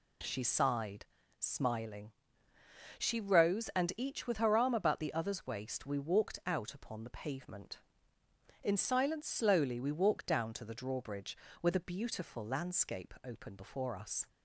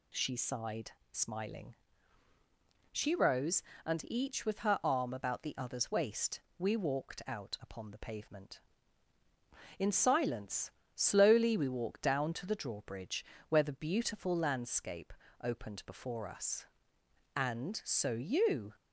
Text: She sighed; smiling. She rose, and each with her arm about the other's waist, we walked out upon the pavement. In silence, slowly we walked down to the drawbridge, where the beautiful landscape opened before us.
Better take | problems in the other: first | pauses between "landscape" and "opened"; slight; at 15.1 s; 0.30 s long // goes on to say "And so you"; from 17.3 s on; 1.4 s long

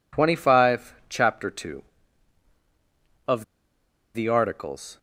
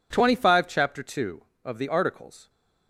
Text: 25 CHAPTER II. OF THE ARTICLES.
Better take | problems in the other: second | pauses between "OF" and "THE"; noticeable; at 3.4 s; 0.70 s long

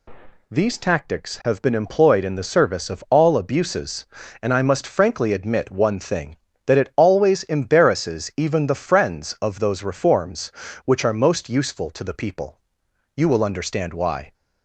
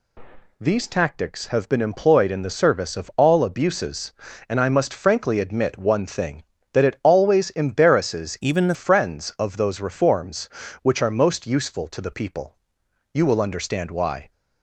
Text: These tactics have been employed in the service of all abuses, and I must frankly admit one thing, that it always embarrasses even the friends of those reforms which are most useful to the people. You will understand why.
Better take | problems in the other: first | changes voice from "even" to "the"; from 8.4 to 8.7 s; 0.3 s long

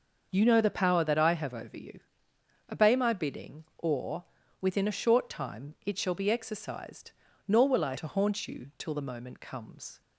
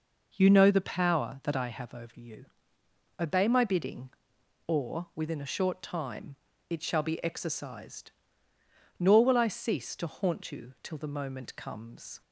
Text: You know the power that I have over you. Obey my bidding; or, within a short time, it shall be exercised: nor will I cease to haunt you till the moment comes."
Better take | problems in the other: second | starts louder than the rest; until 1.3 s; 6.5 dB // skips "cease"; at 7.9 s

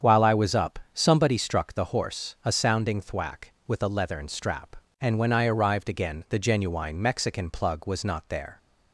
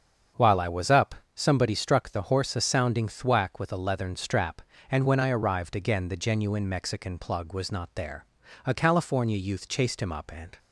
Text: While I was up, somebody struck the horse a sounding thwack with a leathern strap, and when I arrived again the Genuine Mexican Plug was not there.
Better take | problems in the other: first | starts louder than the rest; strong; until 1.5 s; 7 dB; strong in the first // goes on to say "A California youth chased him up and"; strong; from 8.6 s on; 1.9 s long

